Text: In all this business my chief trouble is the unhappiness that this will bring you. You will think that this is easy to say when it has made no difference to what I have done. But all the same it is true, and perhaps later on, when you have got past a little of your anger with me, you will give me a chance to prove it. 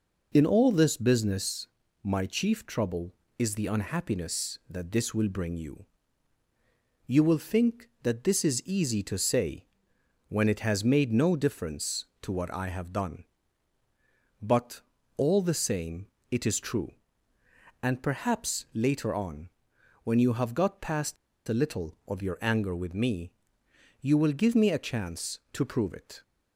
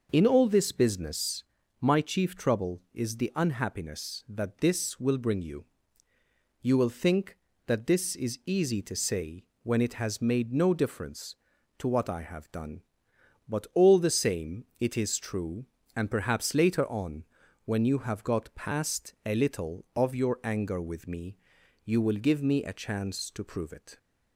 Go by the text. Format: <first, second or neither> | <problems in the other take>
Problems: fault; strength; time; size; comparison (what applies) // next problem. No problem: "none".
second | pauses between "business" and "my"; slight; at 1.6 s; 0.36 s long; slight in the second // pauses between "say" and "when"; noticeable; at 9.6 s; 0.62 s long; slight in the second // pauses between "But" and "all"; slight; at 14.8 s; 0.36 s long // pauses between "same" and "it"; slight; at 16.0 s; 0.24 s long; slight in the second // pauses between "past" and "a"; slight; at 21.1 s; 0.32 s long